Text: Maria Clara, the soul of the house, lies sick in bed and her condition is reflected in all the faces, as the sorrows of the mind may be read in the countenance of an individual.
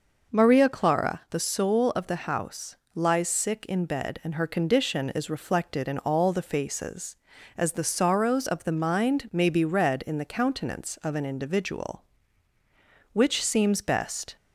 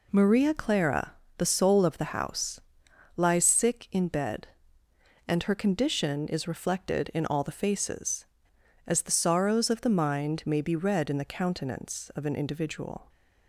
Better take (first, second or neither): second